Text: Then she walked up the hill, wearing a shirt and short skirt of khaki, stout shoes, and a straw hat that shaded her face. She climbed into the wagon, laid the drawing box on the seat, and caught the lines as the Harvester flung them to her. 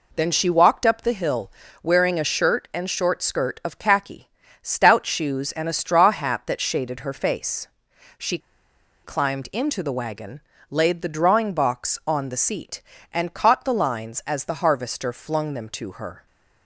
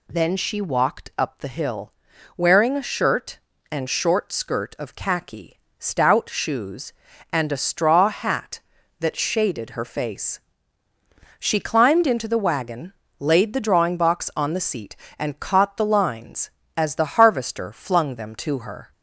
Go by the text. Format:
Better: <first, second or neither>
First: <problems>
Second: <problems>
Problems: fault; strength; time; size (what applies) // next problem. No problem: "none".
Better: second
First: pauses between "She" and "climbed"; noticeable; at 8.3 s; 0.66 s long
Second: none